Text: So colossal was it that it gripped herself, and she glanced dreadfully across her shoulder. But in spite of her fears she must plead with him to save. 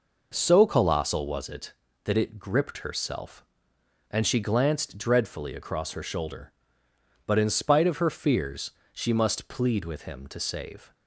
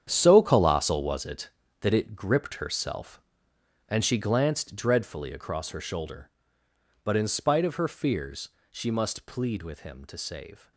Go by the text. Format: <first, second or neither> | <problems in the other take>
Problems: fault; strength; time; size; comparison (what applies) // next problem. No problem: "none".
first | gets quieter; strong; throughout; 12.5 dB // pauses between "fears" and "she"; slight; at 8.4 s; 0.22 s long; slight in the first